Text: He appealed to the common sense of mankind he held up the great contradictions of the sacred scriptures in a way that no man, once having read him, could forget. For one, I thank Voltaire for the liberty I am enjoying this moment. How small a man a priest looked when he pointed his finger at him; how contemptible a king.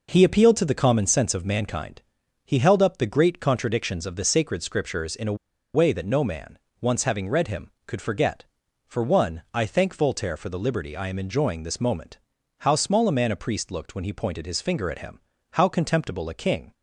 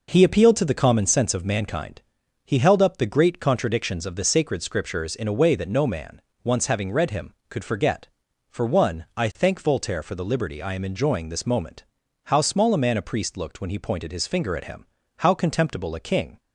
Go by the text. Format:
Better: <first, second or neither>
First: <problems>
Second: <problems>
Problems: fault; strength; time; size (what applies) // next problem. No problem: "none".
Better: second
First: pauses between "mankind" and "he"; at 2.0 s; 0.42 s long // pauses between "a" and "way"; at 5.3 s; 0.39 s long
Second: pauses between "mankind" and "he"; at 2.0 s; 0.42 s long